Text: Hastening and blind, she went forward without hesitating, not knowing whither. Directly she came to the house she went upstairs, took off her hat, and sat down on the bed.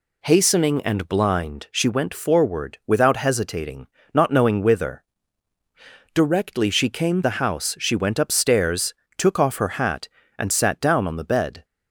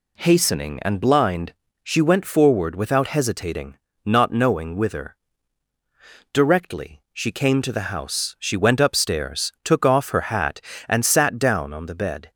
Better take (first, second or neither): second